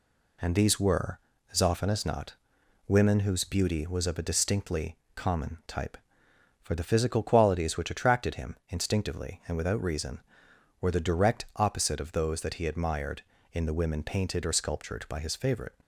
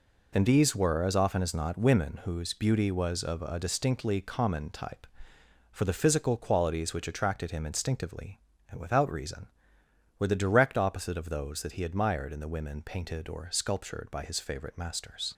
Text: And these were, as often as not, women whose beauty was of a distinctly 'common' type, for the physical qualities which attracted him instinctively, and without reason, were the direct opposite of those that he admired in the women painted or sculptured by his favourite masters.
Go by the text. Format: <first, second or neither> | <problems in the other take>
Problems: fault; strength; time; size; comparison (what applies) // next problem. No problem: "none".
second | pauses between "distinctly" and "common"; slight; at 4.9 s; 0.20 s long // stops before "masters"; at 15.8 s